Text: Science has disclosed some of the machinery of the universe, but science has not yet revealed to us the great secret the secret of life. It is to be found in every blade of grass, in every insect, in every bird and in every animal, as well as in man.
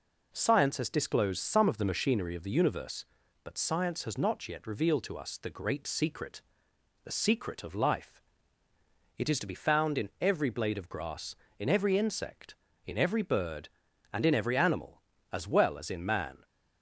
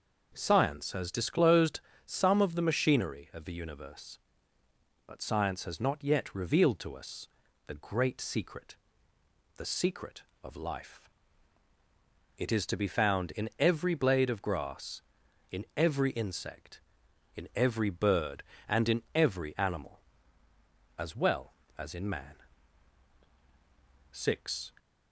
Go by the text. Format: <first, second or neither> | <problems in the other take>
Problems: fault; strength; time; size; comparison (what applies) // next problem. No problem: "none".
first | pauses between "disclosed" and "some"; slight; at 1.7 s; 0.26 s long // pauses between "us" and "the"; at 7.2 s; 0.40 s long // pauses between "secret" and "the"; noticeable; at 8.7 s; 0.82 s long; noticeable in the first // goes on to say "Six"; noticeable; from 24.1 s on; 0.62 s long